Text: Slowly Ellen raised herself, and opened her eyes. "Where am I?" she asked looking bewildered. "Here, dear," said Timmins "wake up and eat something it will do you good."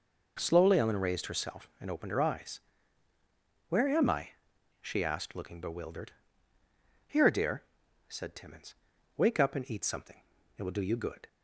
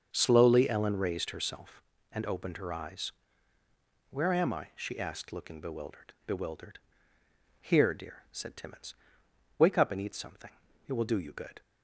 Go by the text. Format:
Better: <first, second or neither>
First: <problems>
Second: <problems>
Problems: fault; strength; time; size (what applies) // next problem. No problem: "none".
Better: first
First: pauses between "Timmins" and "wake"; at 8.7 s; 0.40 s long // pauses between "something" and "it"; slight; at 10.2 s; 0.34 s long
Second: starts louder than the rest; until 1.1 s; 6.5 dB // says "bewildered" twice; at 6.2 s // pauses between "Timmins" and "wake"; noticeable; at 8.9 s; 0.64 s long // pauses between "something" and "it"; at 10.5 s; 0.38 s long